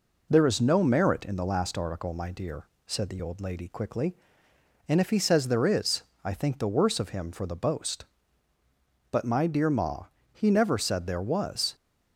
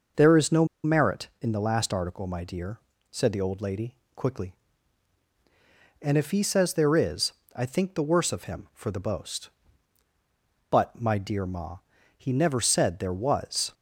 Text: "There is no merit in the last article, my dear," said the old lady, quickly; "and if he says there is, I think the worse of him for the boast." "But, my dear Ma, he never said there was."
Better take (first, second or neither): first